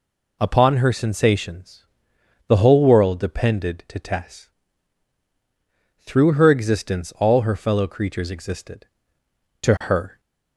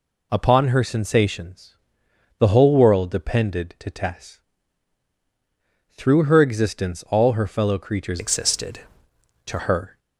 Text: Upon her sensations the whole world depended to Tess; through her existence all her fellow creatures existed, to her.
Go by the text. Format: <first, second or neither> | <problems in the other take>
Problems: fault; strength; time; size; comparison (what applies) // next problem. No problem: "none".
first | pauses between "sensations" and "the"; noticeable; at 1.7 s; 0.62 s long; noticeable in the first // changes voice from "existed" to "to"; from 8.1 to 9.5 s; 1.4 s long